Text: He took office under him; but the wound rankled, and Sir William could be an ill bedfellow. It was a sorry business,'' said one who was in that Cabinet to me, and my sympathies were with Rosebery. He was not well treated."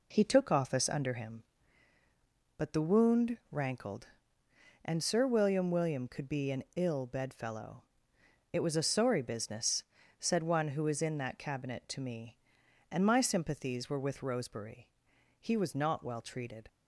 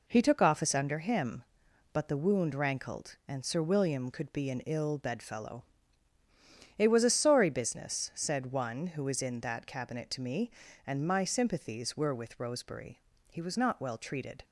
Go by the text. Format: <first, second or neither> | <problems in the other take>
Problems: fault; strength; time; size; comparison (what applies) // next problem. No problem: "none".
second | says "William" twice; at 5.7 s